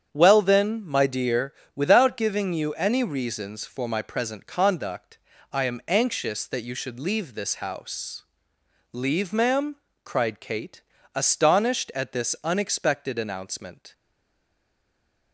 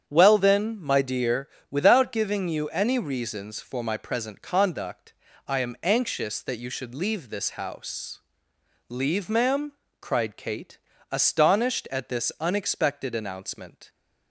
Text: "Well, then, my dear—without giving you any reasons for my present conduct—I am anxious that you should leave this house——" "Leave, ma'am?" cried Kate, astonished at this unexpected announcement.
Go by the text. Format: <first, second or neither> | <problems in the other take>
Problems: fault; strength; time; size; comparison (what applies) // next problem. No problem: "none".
second | starts louder than the rest; strong; until 1.1 s; 8.5 dB; strong in the second // stays silent after the last word; noticeable; from 13.9 s on; 1.4 s long